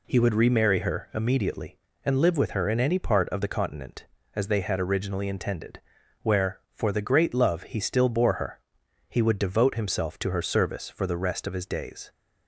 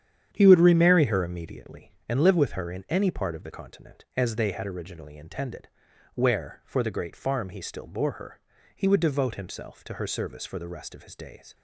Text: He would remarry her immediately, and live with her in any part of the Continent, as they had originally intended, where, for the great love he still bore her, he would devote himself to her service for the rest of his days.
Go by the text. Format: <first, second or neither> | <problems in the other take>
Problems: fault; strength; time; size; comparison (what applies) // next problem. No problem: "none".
first | starts louder than the rest; strong; until 1.3 s; 9 dB // says "farm" for "love"; at 7.1 s